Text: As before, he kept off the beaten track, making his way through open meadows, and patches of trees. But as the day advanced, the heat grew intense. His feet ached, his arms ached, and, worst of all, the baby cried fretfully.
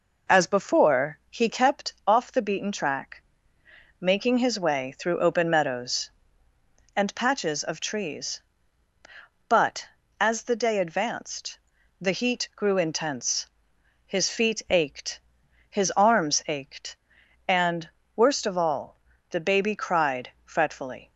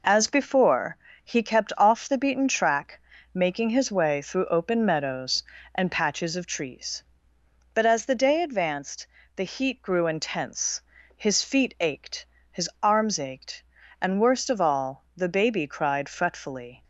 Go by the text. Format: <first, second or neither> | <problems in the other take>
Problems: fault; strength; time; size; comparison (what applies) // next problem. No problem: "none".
neither | none